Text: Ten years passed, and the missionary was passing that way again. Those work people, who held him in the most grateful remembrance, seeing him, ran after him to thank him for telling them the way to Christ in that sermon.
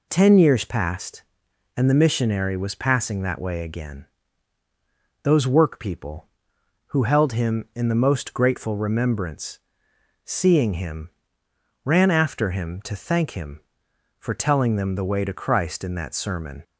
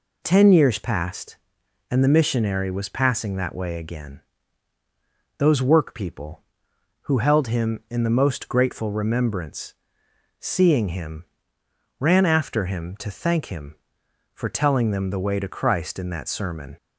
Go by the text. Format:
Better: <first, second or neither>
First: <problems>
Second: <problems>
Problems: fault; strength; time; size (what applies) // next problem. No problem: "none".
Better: neither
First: none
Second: none